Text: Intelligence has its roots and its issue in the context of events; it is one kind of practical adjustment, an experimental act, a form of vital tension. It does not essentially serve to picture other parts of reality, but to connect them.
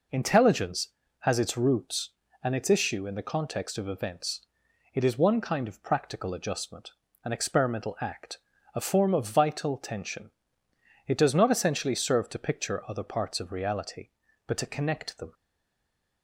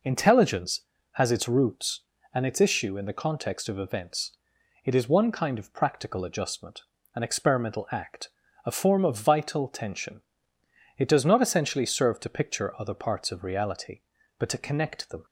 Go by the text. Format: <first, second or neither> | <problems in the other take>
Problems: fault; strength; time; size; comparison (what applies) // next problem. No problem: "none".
second | stays silent after the last word; slight; from 15.3 s on; 0.9 s long